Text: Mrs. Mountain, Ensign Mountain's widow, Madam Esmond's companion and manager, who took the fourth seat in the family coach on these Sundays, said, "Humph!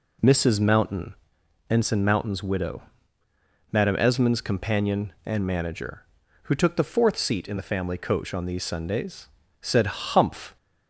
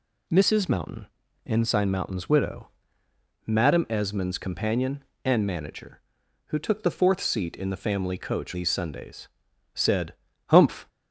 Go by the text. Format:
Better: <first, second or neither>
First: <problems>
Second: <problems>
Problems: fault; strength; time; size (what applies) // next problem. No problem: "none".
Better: first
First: none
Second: skips "on"; at 8.5 s